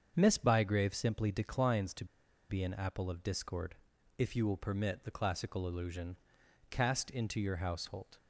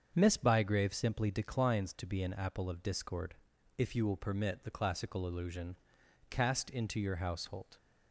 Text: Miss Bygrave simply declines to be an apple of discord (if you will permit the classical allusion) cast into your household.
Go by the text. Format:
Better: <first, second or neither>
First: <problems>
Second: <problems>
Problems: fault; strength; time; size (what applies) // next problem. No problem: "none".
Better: second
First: starts louder than the rest; until 1.1 s; 7 dB // pauses between "to" and "be"; at 2.0 s; 0.44 s long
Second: starts louder than the rest; until 1.1 s; 7 dB